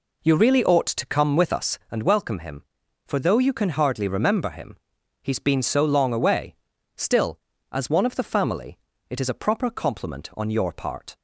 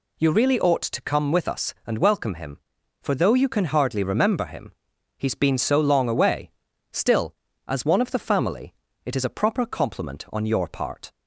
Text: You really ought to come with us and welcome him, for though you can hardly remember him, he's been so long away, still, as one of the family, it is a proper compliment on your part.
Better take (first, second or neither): second